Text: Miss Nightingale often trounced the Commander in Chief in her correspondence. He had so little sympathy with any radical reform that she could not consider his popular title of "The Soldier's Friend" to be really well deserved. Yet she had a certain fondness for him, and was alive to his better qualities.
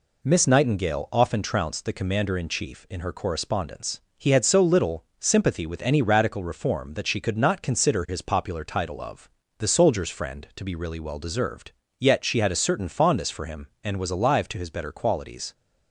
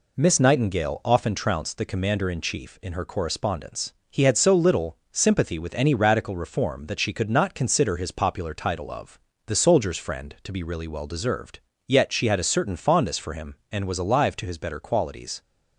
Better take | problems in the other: neither | pauses between "of" and "The"; slight; the same in both

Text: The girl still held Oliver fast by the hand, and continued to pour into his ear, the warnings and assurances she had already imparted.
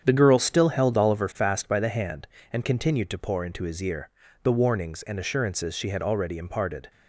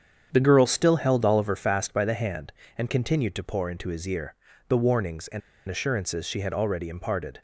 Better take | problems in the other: first | starts louder than the rest; strong; until 1.3 s; 8 dB; strong in the first // pauses between "and" and "assurances"; slight; at 5.4 s; 0.28 s long

